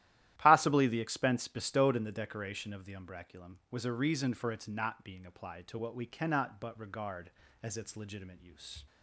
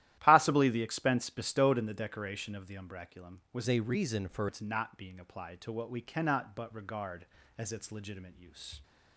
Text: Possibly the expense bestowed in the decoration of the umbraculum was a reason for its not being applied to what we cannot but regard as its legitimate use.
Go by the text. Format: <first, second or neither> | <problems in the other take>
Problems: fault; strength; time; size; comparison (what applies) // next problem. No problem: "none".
first | starts louder than the rest; strong; until 1.2 s; 13.5 dB; strong in the first // changes voice from "a" to "for"; from 3.6 to 4.4 s; 0.8 s long